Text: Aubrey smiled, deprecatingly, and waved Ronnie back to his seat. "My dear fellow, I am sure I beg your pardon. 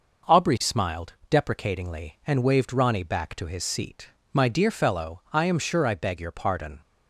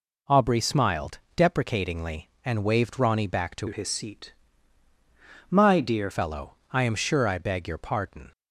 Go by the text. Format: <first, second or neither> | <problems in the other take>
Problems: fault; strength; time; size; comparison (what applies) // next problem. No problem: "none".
first | changes voice from "his" to "dear"; from 3.6 to 6.0 s; 2.4 s long